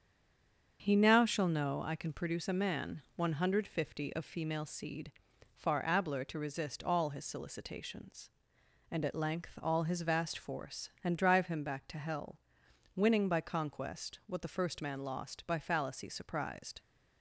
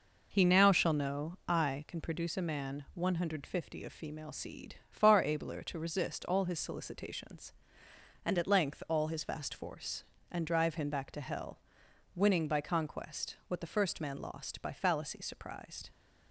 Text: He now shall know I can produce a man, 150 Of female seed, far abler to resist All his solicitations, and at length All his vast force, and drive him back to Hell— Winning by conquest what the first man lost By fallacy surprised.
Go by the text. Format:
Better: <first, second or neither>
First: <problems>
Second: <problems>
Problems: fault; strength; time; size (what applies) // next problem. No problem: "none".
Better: second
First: stays silent before the first word; slight; until 0.7 s; 0.7 s long // starts louder than the rest; strong; until 1.8 s; 7.5 dB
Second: none